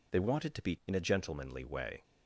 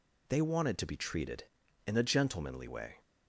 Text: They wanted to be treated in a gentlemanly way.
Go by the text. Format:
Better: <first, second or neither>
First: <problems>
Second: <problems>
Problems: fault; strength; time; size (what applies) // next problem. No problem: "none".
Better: second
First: skips "treated"; at 0.8 s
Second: none